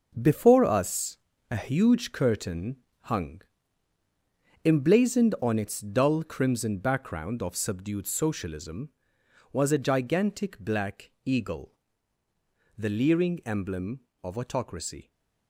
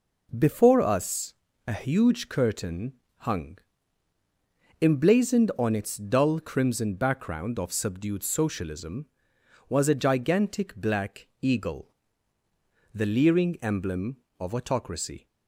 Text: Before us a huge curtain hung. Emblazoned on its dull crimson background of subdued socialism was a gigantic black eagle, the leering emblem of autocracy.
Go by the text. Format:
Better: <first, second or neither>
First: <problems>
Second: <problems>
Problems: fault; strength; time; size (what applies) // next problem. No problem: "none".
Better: second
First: gets quieter; strong; throughout; 9 dB // pauses between "us" and "a"; slight; at 1.1 s; 0.32 s long // pauses between "curtain" and "hung"; slight; at 2.7 s; 0.26 s long // pauses between "black" and "eagle"; slight; at 11.0 s; 0.16 s long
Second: pauses between "us" and "a"; slight; at 1.3 s; 0.32 s long // pauses between "curtain" and "hung"; slight; at 2.9 s; 0.26 s long // pauses between "black" and "eagle"; slight; at 11.2 s; 0.16 s long